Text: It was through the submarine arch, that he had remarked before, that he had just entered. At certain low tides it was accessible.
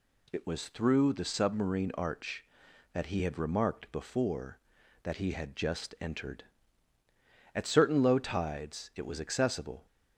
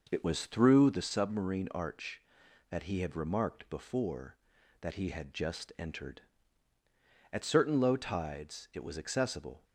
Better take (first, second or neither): first